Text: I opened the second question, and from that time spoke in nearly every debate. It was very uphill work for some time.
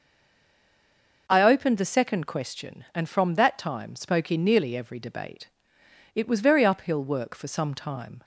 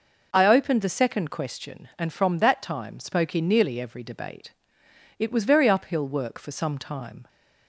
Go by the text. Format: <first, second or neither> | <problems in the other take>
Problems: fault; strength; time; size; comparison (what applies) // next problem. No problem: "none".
second | stays silent before the first word; noticeable; until 1.2 s; 1.2 s long